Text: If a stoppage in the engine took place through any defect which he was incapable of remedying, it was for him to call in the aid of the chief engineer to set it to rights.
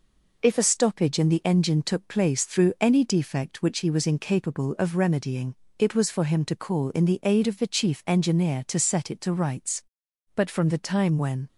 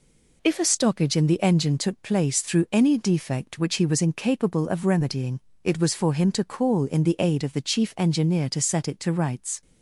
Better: second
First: goes on to say "But from the time when"; noticeable; from 10.3 s on; 1.1 s long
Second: none

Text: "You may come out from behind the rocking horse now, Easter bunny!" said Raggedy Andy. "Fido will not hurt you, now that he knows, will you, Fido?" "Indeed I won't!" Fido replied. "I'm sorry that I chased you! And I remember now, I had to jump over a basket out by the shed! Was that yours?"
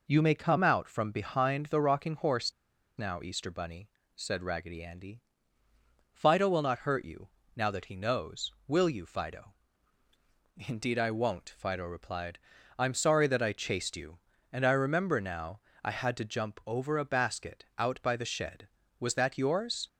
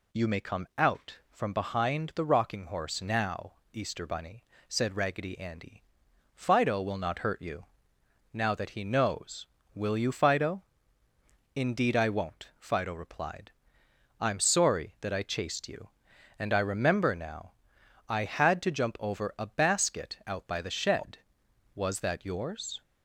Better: second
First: pauses between "horse" and "now"; at 2.5 s; 0.45 s long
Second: none

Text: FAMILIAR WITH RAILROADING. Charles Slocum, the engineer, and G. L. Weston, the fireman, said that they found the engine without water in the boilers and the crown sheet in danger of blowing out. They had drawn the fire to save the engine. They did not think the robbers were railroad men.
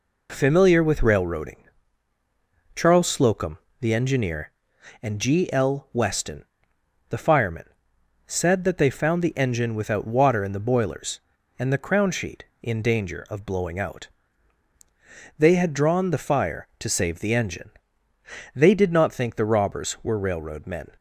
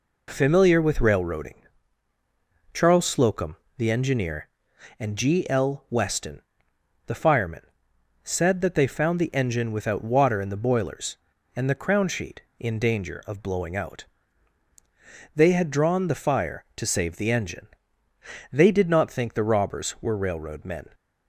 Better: neither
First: none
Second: none

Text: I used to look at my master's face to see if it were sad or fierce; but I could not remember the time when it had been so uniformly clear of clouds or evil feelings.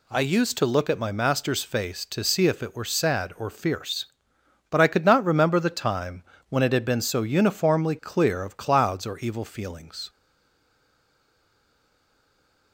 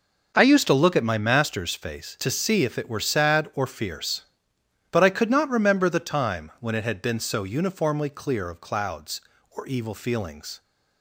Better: second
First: pauses between "time" and "when"; slight; at 6.2 s; 0.26 s long // stays silent after the last word; strong; from 10.0 s on; 2.7 s long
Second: none

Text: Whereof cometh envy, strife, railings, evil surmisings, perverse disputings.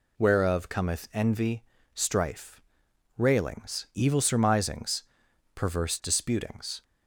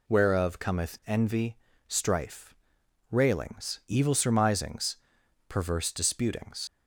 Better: first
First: none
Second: leaves "disputings" unfinished; at 6.6 s; 75 ms

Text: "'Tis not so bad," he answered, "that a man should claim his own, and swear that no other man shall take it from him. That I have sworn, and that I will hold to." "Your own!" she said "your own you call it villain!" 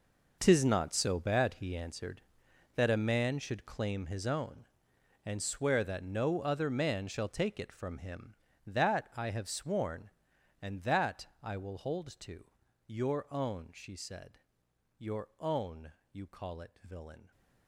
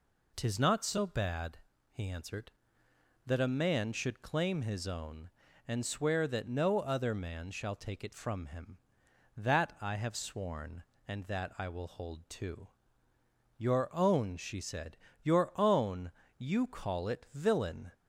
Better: second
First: gets quieter; strong; throughout; 14 dB // pauses between "that" and "I"; slight; at 11.2 s; 0.16 s long // pauses between "said" and "your"; noticeable; at 14.3 s; 0.60 s long // pauses between "own" and "you"; slight; at 15.9 s; 0.20 s long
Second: pauses between "said" and "your"; slight; at 14.9 s; 0.26 s long // pauses between "own" and "you"; slight; at 16.1 s; 0.29 s long

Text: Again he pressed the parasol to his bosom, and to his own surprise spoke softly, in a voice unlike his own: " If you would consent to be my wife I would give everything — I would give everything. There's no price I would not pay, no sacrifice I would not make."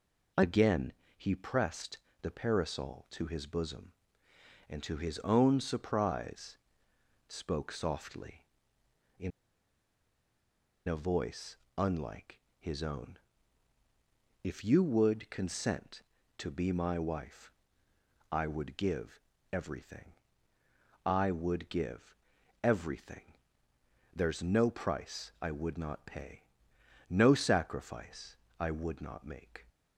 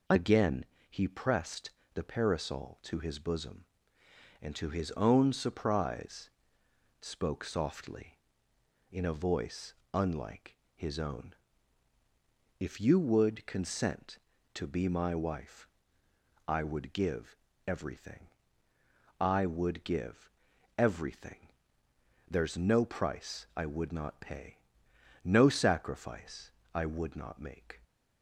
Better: second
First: pauses between "Again" and "he"; slight; at 0.9 s; 0.24 s long // pauses between "pressed" and "the"; slight; at 1.9 s; 0.24 s long // pauses between "surprise" and "spoke"; noticeable; at 6.5 s; 0.70 s long // pauses between "in" and "a"; strong; at 9.3 s; 1.5 s long // pauses between "voice" and "unlike"; slight; at 11.5 s; 0.22 s long // pauses between "unlike" and "his"; slight; at 12.3 s; 0.20 s long // pauses between "wife" and "I"; noticeable; at 17.5 s; 0.80 s long // pauses between "give" and "everything"; slight; at 19.1 s; 0.32 s long // pauses between "give" and "everything"; noticeable; at 22.1 s; 0.48 s long // pauses between "sacrifice" and "I"; slight; at 28.3 s; 0.24 s long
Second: pauses between "Again" and "he"; slight; at 0.6 s; 0.24 s long // pauses between "pressed" and "the"; slight; at 1.7 s; 0.24 s long // pauses between "surprise" and "spoke"; noticeable; at 6.3 s; 0.70 s long // pauses between "voice" and "unlike"; slight; at 9.7 s; 0.21 s long // pauses between "unlike" and "his"; slight; at 10.5 s; 0.20 s long // pauses between "wife" and "I"; noticeable; at 15.6 s; 0.80 s long // pauses between "give" and "everything"; slight; at 17.3 s; 0.30 s long // pauses between "give" and "everything"; noticeable; at 20.2 s; 0.48 s long // pauses between "sacrifice" and "I"; slight; at 26.4 s; 0.24 s long

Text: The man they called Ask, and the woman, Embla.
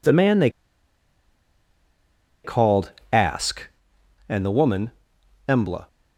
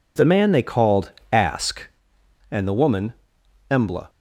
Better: second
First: pauses between "they" and "called"; strong; at 0.5 s; 1.9 s long // pauses between "called" and "Ask"; slight; at 2.9 s; 0.20 s long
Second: pauses between "called" and "Ask"; slight; at 1.1 s; 0.20 s long

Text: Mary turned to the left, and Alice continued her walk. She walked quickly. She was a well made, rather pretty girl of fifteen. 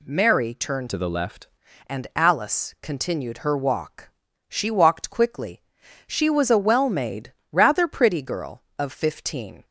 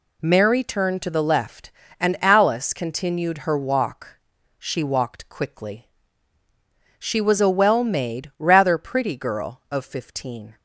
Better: second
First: changes voice from "to" to "left"; from 0.8 to 1.4 s; 0.6 s long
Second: none

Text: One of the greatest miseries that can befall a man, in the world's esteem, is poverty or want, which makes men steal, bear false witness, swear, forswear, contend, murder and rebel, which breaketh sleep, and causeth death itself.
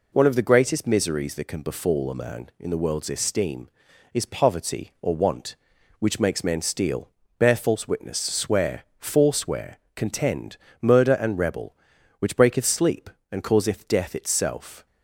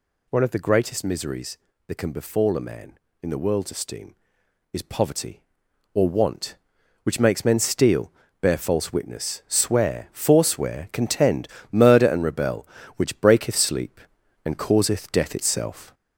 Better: first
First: none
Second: gets louder; noticeable; throughout; 4 dB

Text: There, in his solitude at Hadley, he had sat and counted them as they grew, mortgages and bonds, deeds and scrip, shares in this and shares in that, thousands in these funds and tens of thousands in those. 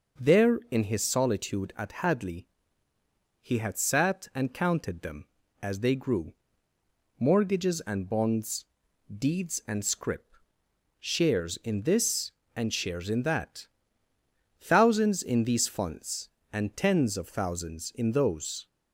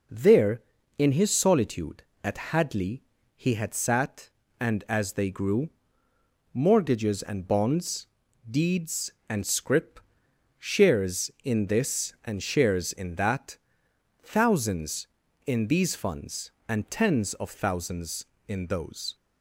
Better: first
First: none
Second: skips "counted them"; at 4.8 s

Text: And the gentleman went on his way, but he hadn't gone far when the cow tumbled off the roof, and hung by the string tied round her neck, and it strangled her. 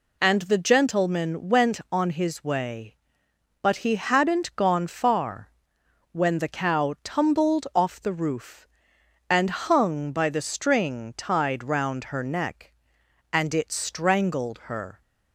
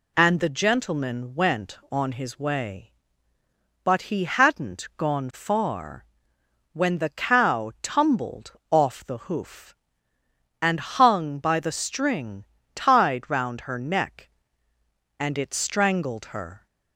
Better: first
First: pauses between "far" and "when"; noticeable; at 5.5 s; 0.60 s long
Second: pauses between "far" and "when"; noticeable; at 6.0 s; 0.66 s long // pauses between "tumbled" and "off"; slight; at 8.5 s; 0.18 s long // says "hoof" for "roof"; at 9.2 s // pauses between "string" and "tied"; slight; at 12.4 s; 0.30 s long

